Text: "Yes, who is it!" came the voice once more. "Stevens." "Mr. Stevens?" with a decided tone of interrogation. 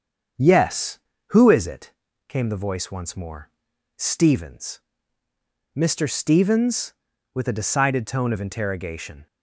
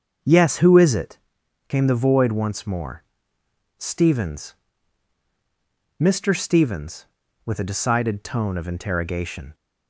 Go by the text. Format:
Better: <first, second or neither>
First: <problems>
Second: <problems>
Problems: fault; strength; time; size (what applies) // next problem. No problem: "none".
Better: first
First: starts louder than the rest; strong; until 1.6 s; 7 dB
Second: starts louder than the rest; until 1.7 s; 7 dB // says "void" for "voice"; at 1.9 s